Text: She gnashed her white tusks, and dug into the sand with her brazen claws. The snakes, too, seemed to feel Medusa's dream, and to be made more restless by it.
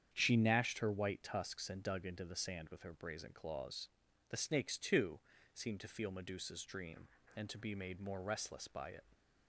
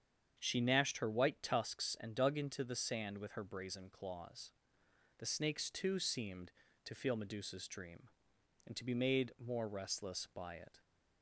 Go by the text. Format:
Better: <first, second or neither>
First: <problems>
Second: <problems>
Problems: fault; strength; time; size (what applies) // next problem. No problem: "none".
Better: neither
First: starts louder than the rest; strong; until 1.1 s; 8.5 dB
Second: starts louder than the rest; strong; until 1.4 s; 7.5 dB